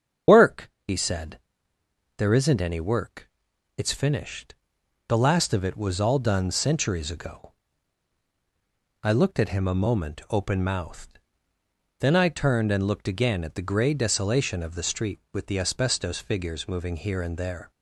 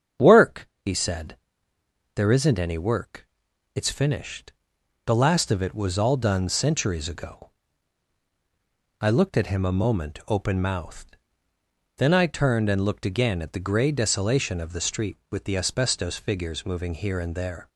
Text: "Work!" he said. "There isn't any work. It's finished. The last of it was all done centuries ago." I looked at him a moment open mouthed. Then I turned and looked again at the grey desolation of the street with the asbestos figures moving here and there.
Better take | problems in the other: second | loses the start of "Work"; at 0.2 s; 60 ms // starts louder than the rest; strong; until 2.2 s; 8 dB; strong in the second

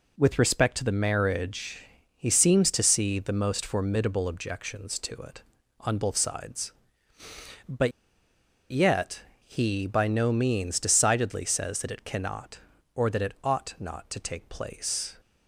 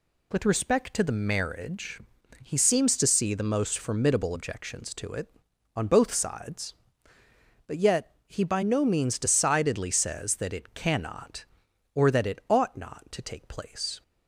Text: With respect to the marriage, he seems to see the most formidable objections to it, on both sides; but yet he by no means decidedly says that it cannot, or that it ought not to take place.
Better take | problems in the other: second | pauses between "but" and "yet"; noticeable; at 7.9 s; 0.81 s long // pauses between "yet" and "he"; slight; at 9.2 s; 0.26 s long

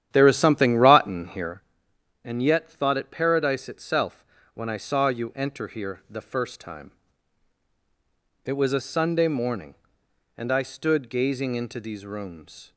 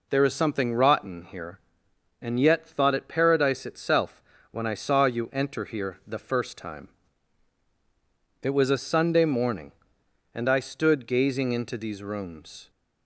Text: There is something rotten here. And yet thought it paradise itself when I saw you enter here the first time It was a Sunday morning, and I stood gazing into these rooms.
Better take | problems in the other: second | starts louder than the rest; strong; until 1.6 s; 10.5 dB // pauses between "itself" and "when"; slight; at 4.2 s; 0.28 s long; slight in the second // pauses between "time" and "It"; strong; at 6.9 s; 1.5 s long; strong in the second

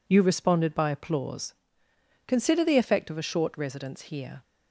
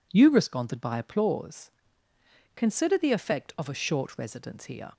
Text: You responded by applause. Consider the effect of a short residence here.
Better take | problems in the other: neither | none

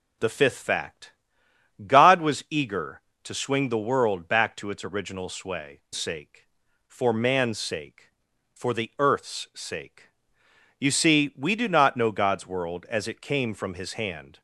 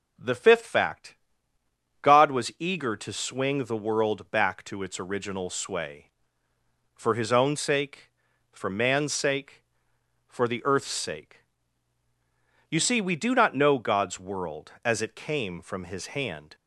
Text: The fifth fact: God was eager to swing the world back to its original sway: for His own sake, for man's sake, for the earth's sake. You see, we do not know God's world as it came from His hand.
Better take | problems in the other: second | skips "for His own"; at 5.8 s

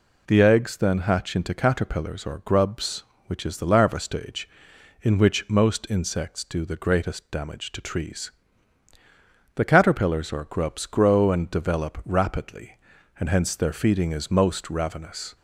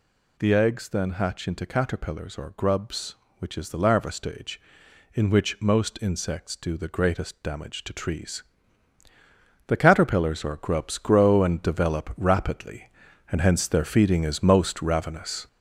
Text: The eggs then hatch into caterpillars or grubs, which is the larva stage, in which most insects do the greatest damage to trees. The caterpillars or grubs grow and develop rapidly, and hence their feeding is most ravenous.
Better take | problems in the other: first | gets louder; noticeable; throughout; 5 dB

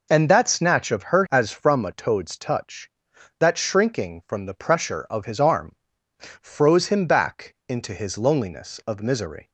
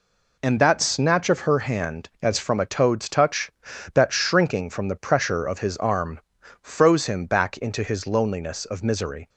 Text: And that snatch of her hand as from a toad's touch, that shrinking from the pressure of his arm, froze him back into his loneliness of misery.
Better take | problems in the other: second | skips "hand"; at 1.2 s

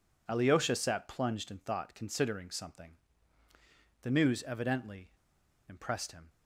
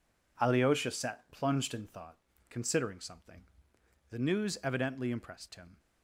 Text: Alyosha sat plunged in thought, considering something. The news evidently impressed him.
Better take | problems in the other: second | pauses between "evidently" and "impressed"; noticeable; at 5.0 s; 0.57 s long

